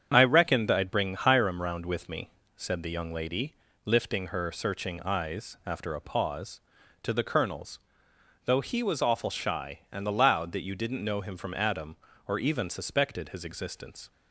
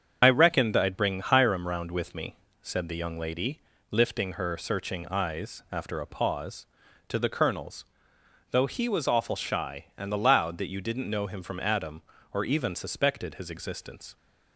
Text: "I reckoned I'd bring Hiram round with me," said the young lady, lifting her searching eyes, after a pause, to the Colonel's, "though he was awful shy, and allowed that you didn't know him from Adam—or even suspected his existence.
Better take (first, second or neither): first